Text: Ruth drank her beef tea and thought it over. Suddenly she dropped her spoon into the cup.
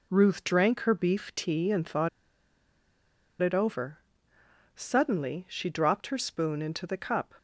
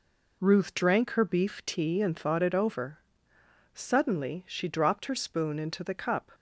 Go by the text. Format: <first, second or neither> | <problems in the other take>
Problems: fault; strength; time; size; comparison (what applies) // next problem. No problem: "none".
second | pauses between "thought" and "it"; strong; at 2.0 s; 1.3 s long